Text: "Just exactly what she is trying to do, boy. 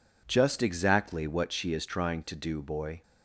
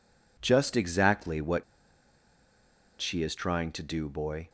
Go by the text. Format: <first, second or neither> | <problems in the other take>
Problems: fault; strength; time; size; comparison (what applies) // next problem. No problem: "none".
first | pauses between "what" and "she"; strong; at 1.6 s; 1.3 s long